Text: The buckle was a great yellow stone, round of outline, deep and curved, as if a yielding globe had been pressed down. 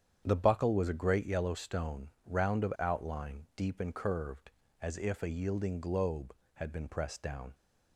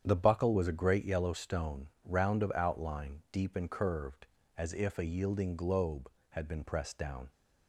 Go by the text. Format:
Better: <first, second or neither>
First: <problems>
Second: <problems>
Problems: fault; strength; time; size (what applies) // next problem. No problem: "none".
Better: neither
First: starts louder than the rest; strong; until 1.2 s; 8.5 dB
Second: starts louder than the rest; strong; until 1.0 s; 8.5 dB